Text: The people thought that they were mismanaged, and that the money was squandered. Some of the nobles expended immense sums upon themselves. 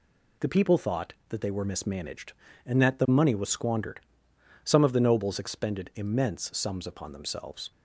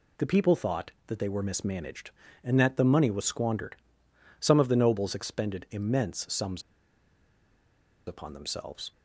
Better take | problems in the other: first | pauses between "sums" and "upon"; strong; at 6.6 s; 1.4 s long

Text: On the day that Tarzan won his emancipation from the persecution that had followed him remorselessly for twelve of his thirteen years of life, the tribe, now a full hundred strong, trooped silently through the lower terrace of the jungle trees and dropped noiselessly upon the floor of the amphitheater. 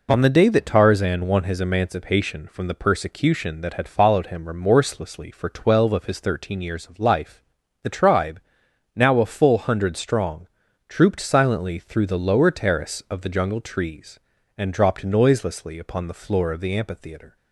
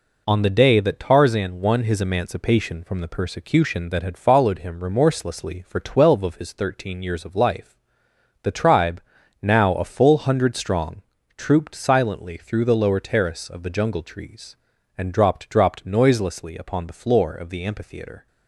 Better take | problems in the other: first | says "dropped" twice; at 15.4 s

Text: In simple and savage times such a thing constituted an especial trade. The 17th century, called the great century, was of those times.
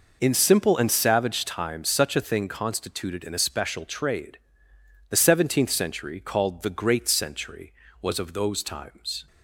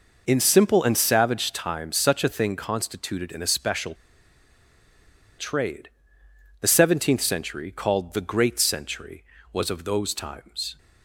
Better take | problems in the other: first | pauses between "especial" and "trade"; strong; at 3.9 s; 1.4 s long

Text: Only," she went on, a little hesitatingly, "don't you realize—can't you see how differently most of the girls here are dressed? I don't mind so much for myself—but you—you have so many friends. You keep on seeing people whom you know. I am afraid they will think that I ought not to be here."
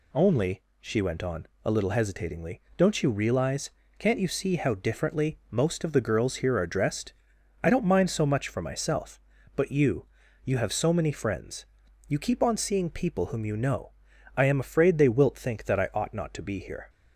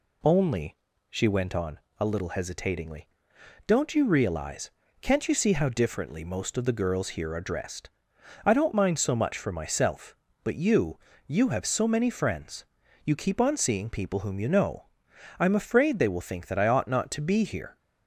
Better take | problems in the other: second | says "wilt" for "will"; at 15.0 s

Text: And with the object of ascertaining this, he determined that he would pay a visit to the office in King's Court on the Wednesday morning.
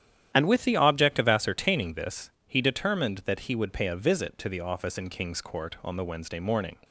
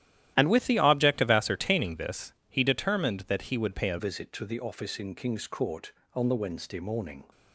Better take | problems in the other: first | starts louder than the rest; strong; until 1.3 s; 12.5 dB; strong in the first // changes voice at "visit"; from 3.9 s on; 3.3 s long

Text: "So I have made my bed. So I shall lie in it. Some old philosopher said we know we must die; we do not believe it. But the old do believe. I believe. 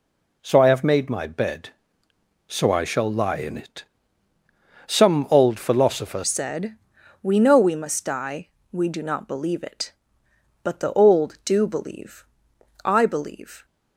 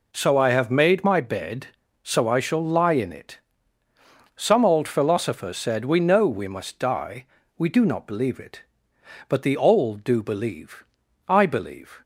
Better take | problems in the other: second | changes voice at "said"; from 6.2 s on; 7.4 s long // pauses between "said" and "we"; noticeable; at 6.7 s; 0.48 s long

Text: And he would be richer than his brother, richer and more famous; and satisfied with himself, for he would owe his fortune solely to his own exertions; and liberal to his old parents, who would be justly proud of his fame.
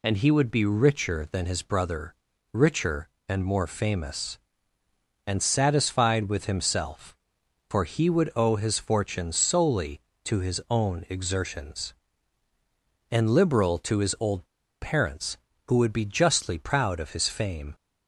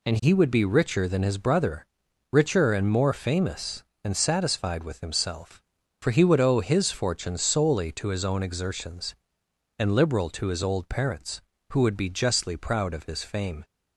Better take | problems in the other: second | pauses between "old" and "parents"; at 14.4 s; 0.36 s long

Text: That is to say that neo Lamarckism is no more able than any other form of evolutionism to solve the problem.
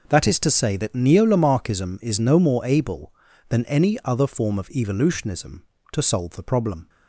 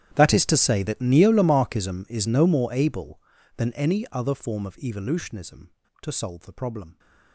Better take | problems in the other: first | gets quieter; strong; throughout; 22.5 dB

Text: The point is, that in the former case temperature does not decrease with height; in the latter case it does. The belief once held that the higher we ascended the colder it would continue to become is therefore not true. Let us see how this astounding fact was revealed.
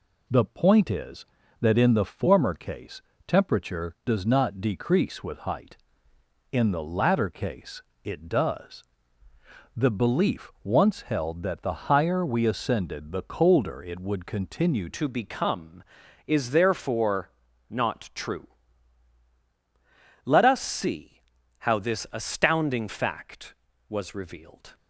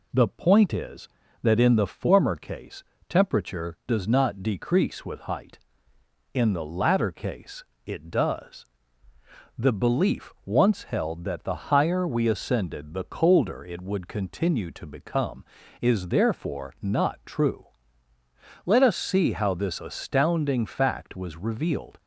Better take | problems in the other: second | pauses between "case" and "temperature"; slight; at 3.0 s; 0.26 s long; slight in the second // pauses between "case" and "it"; slight; at 7.8 s; 0.22 s long; slight in the second // changes voice at "to"; from 14.9 s on; 9.8 s long // pauses between "therefore" and "not"; at 17.2 s; 0.40 s long // pauses between "see" and "how"; at 21.1 s; 0.40 s long

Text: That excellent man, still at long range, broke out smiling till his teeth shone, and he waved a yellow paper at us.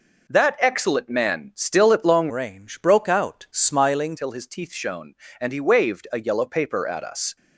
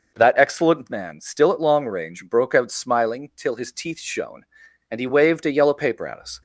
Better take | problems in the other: second | changes voice from "range" to "smiling"; from 2.2 to 4.1 s; 1.9 s long

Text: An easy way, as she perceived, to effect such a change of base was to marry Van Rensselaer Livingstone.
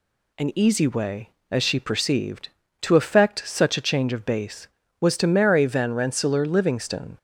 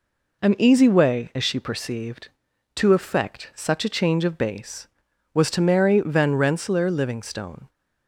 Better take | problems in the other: neither | none

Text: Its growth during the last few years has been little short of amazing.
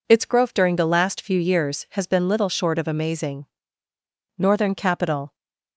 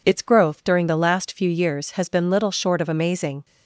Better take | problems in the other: second | goes on to say "Northern capital"; noticeable; from 4.3 s on; 0.98 s long

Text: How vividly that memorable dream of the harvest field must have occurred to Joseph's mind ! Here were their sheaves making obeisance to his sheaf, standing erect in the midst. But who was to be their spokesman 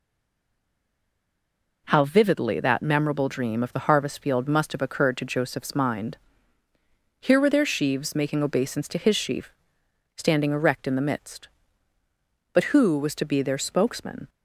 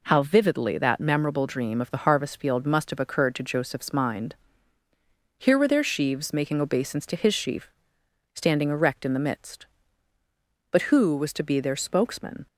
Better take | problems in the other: second | stays silent before the first word; noticeable; until 1.8 s; 1.8 s long

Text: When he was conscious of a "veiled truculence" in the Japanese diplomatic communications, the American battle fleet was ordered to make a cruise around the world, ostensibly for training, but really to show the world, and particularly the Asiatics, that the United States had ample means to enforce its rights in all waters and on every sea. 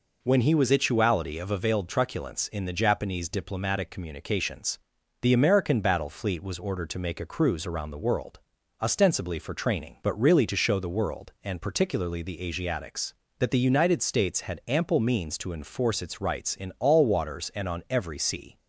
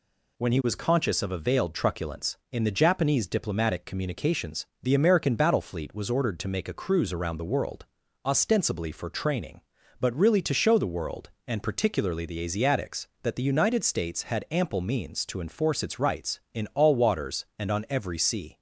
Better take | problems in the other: second | says "ituality" for "conscious"; at 0.7 s

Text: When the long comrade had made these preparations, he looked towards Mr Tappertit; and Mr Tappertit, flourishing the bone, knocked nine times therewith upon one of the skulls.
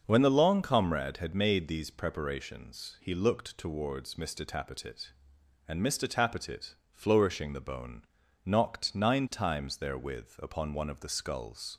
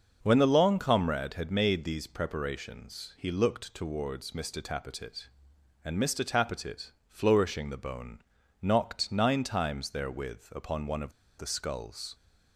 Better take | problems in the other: first | starts louder than the rest; until 1.2 s; 6 dB; also in the first // pauses between "of" and "the"; slight; at 11.1 s; 0.25 s long

